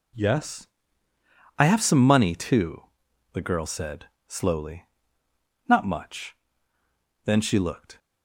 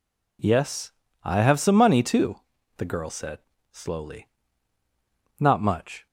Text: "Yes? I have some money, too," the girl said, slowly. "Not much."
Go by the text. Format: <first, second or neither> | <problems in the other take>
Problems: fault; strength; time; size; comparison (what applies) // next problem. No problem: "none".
second | goes on to say "Then she looked"; noticeable; from 7.2 s on; 0.74 s long